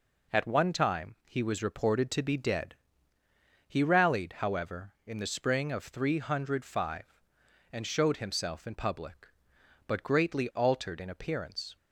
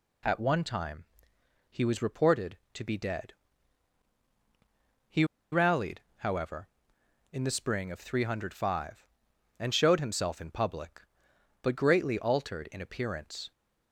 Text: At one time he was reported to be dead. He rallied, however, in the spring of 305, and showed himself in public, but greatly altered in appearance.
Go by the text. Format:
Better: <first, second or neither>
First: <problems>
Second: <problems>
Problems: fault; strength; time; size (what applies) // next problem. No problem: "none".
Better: first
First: none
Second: pauses between "time" and "he"; noticeable; at 1.0 s; 0.66 s long // pauses between "He" and "rallied"; slight; at 5.2 s; 0.28 s long